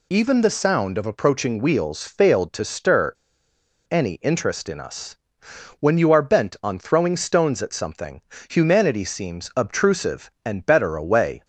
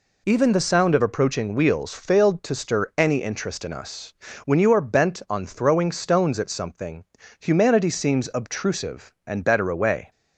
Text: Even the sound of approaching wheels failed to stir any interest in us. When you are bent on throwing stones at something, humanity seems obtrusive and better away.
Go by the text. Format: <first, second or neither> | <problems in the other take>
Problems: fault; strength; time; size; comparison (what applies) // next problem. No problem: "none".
second | pauses between "stir" and "any"; noticeable; at 3.1 s; 0.77 s long